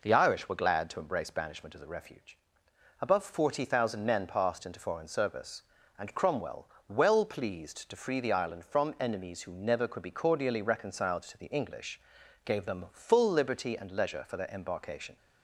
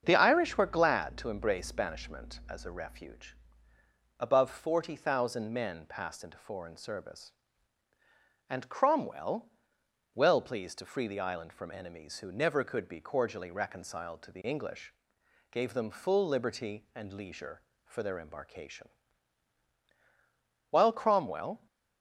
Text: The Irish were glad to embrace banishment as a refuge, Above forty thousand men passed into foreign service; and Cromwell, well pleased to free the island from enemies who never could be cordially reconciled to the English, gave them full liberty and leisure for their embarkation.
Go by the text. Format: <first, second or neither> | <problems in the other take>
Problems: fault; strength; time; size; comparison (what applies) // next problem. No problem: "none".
first | starts louder than the rest; until 1.0 s; 7 dB // goes on to say "While Cromwell"; noticeable; from 20.7 s on; 0.96 s long